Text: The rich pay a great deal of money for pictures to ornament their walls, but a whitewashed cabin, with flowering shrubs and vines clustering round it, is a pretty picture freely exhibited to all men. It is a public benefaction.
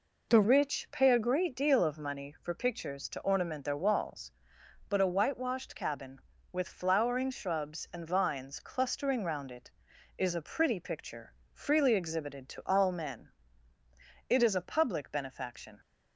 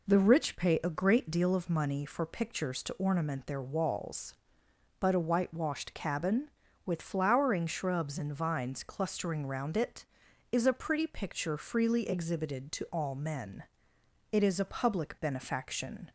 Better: second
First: changes voice at "rich"; from 0.4 s on; 15.3 s long // pauses between "picture" and "freely"; slight; at 11.3 s; 0.22 s long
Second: none

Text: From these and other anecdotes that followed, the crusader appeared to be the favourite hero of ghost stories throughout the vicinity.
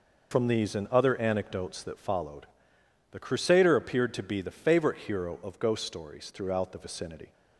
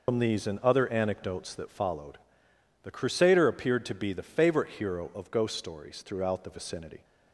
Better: first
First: none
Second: loses the start of "From"; at 0.0 s; 55 ms

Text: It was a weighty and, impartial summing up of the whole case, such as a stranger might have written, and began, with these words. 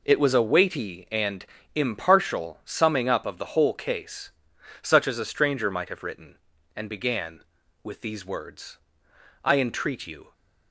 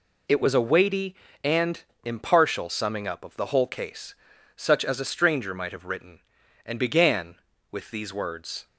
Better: second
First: goes on to say "I entreat you"; noticeable; from 9.4 s on; 0.88 s long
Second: none

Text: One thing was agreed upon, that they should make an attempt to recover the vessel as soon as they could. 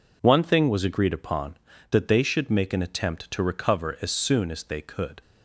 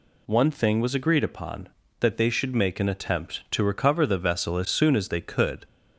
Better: second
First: skips "the vessel"; at 3.9 s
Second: none

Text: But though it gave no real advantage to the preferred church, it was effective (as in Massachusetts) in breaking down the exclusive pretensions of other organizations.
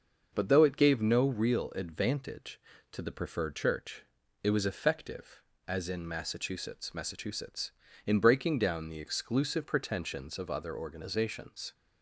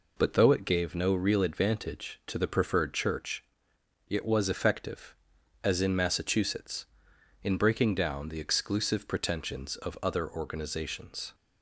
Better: second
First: starts louder than the rest; until 1.3 s; 6 dB // says "Massachusetts" twice; at 6.9 s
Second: none

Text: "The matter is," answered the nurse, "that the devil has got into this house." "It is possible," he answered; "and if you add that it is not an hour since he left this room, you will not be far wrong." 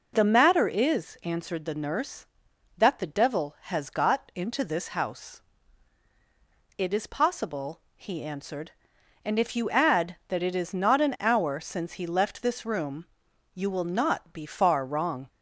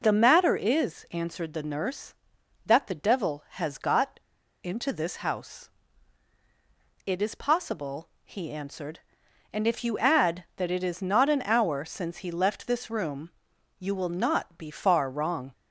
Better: first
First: none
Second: pauses between "got" and "into"; noticeable; at 4.1 s; 0.46 s long

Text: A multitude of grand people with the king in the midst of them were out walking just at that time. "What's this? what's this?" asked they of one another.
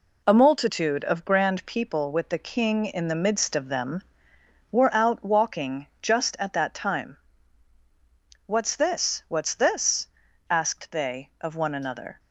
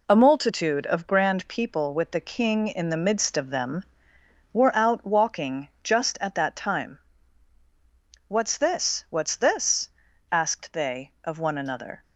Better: neither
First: none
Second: none

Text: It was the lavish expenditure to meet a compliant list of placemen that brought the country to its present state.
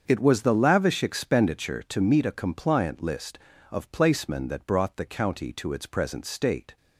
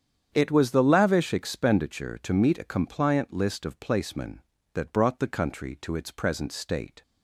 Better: second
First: starts louder than the rest; until 1.0 s; 7 dB // says "county" for "country"; at 5.0 s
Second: starts louder than the rest; strong; until 1.3 s; 8 dB

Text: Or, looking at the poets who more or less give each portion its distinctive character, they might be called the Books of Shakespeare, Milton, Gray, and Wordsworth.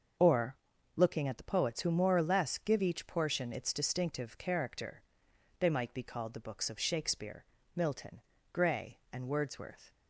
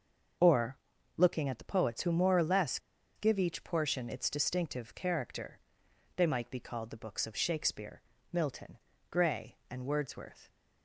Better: first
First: starts louder than the rest; until 1.5 s; 6 dB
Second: starts louder than the rest; until 1.7 s; 6 dB // pauses between "less" and "give"; at 2.7 s; 0.37 s long

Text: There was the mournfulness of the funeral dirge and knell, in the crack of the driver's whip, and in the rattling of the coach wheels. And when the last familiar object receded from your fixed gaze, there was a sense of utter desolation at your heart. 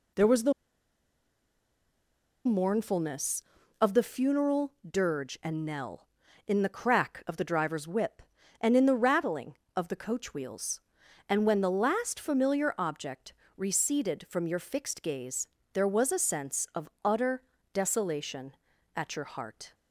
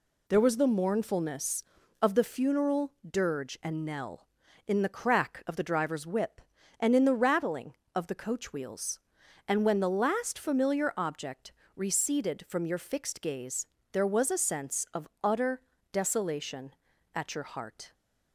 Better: second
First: pauses between "the" and "mournfulness"; strong; at 0.5 s; 1.9 s long // pauses between "funeral" and "dirge"; slight; at 4.7 s; 0.16 s long // pauses between "object" and "receded"; slight; at 13.3 s; 0.24 s long // pauses between "of" and "utter"; slight; at 16.8 s; 0.16 s long // pauses between "utter" and "desolation"; slight; at 17.4 s; 0.30 s long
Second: pauses between "funeral" and "dirge"; slight; at 2.9 s; 0.16 s long // pauses between "object" and "receded"; slight; at 11.5 s; 0.24 s long // pauses between "of" and "utter"; slight; at 15.0 s; 0.16 s long // pauses between "utter" and "desolation"; slight; at 15.6 s; 0.30 s long

